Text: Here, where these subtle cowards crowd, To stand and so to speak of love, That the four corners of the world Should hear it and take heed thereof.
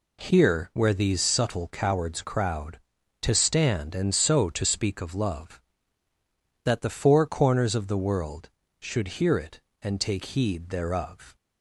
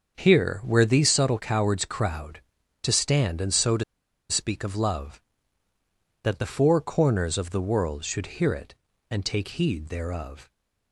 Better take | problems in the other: first | starts louder than the rest; until 1.1 s; 6.5 dB // pauses between "to" and "speak"; noticeable; at 3.8 s; 0.46 s long

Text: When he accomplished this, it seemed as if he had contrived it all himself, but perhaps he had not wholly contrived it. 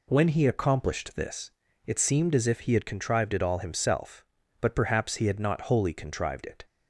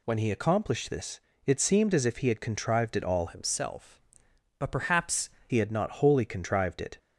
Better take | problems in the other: first | changes voice from "himself" to "perhaps"; from 3.2 to 5.2 s; 2.0 s long

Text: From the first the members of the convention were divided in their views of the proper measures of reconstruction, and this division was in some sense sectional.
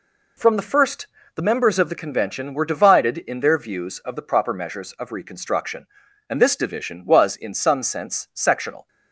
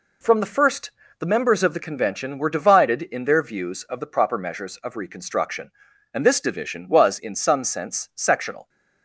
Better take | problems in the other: neither | pauses between "first" and "the"; slight; the same in both

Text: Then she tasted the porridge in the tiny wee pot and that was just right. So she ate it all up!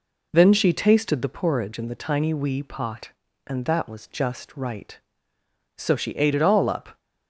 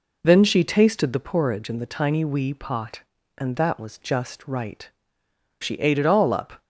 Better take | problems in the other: first | skips "So"; at 5.2 s

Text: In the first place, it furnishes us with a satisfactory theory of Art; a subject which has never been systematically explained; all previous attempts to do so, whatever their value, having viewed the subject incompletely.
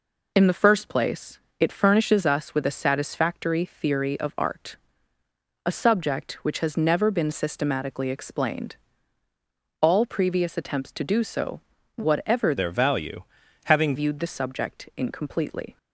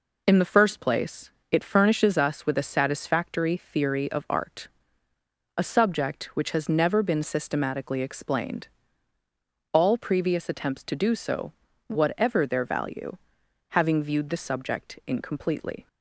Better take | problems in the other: second | changes voice from "their" to "having"; from 12.5 to 13.9 s; 1.4 s long

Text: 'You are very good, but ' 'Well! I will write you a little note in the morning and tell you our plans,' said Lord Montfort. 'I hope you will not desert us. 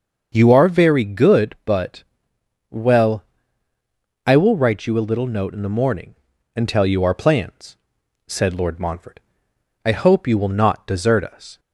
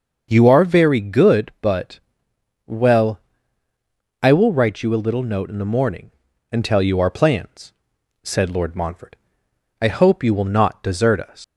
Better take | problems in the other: first | starts louder than the rest; until 1.3 s; 6.5 dB; also in the first // leaves "us" unfinished; at 11.4 s; 110 ms

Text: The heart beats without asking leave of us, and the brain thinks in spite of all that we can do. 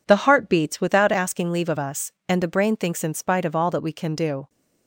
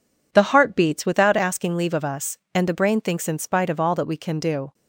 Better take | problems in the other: neither | none

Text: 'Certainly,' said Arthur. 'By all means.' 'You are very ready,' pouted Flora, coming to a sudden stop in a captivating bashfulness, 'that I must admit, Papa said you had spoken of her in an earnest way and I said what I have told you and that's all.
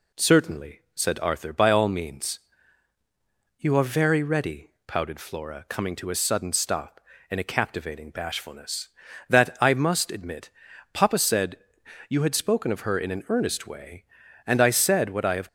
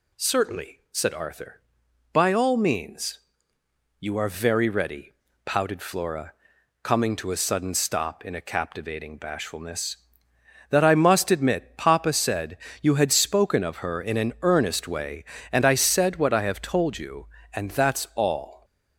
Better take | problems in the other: second | pauses between "said" and "you"; noticeable; at 11.5 s; 0.52 s long; slight in the second // stops before "told you and that's all"; at 15.4 s

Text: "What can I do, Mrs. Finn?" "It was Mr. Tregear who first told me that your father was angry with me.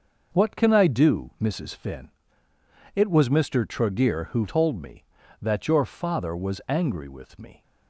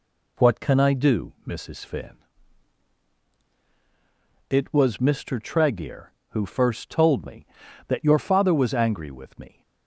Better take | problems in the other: second | skips "first"; at 4.4 s

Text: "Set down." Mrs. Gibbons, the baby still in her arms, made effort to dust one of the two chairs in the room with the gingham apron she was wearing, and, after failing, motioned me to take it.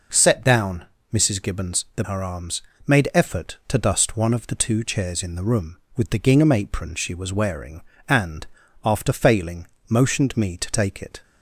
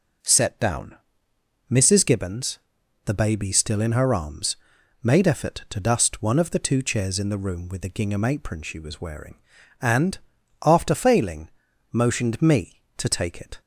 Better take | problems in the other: second | skips "baby still in"; at 2.0 s

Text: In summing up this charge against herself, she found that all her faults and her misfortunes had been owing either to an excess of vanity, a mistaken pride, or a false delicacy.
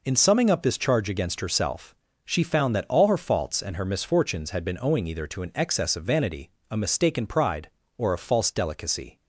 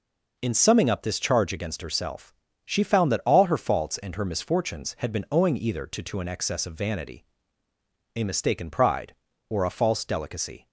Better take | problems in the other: first | says "to" twice; at 6.0 s

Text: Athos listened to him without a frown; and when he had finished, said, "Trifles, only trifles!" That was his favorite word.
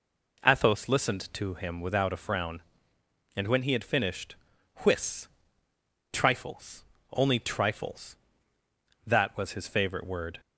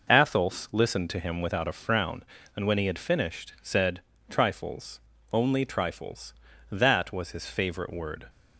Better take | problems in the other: second | says "whiss" for "said"; at 4.8 s

